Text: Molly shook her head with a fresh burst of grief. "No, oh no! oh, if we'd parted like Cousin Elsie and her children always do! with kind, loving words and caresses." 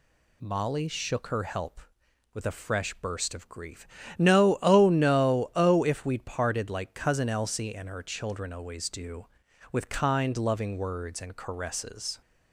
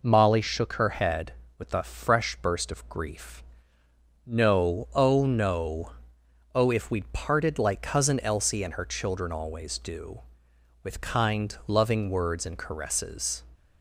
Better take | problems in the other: second | says "help" for "head"; at 1.4 s

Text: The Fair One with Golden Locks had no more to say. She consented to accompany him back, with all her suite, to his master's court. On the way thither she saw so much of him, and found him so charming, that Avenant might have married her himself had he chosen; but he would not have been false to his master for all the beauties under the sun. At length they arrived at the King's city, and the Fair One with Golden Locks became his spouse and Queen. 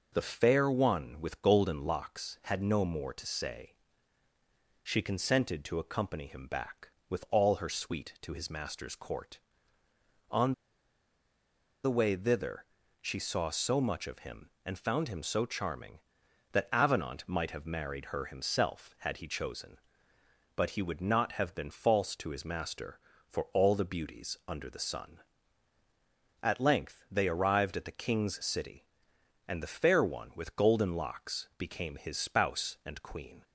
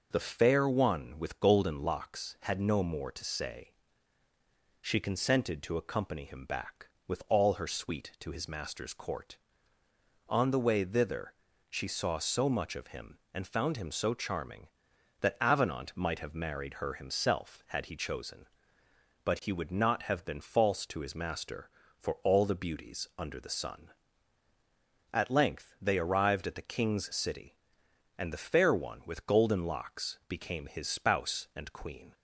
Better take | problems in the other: second | pauses between "On" and "the"; strong; at 10.5 s; 1.3 s long // pauses between "thither" and "she"; at 12.6 s; 0.38 s long; also in the second

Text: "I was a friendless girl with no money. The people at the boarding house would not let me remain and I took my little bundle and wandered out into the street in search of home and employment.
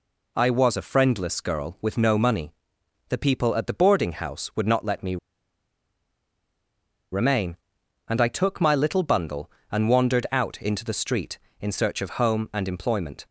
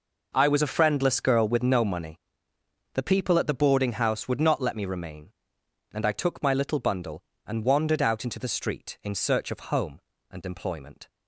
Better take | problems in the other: second | pauses between "me" and "remain"; strong; at 5.1 s; 1.9 s long

